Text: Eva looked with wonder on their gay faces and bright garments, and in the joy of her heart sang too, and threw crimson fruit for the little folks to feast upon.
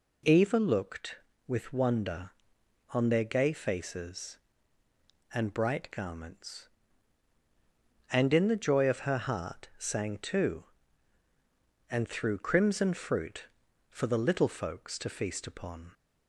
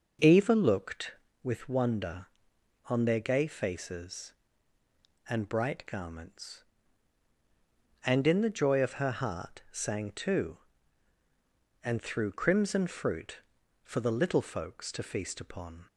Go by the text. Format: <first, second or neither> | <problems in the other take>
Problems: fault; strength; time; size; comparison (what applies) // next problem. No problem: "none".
first | starts louder than the rest; noticeable; until 1.4 s; 5.5 dB